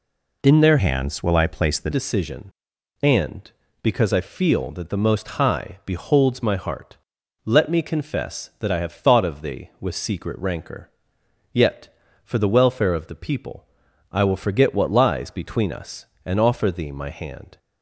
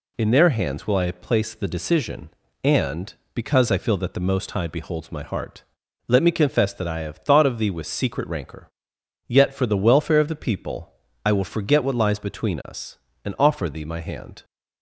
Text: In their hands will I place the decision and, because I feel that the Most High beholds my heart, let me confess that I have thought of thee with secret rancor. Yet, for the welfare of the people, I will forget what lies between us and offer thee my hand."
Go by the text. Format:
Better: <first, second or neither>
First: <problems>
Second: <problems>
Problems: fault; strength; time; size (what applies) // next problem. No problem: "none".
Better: second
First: changes voice from "hands" to "the"; from 0.7 to 1.9 s; 1.2 s long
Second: none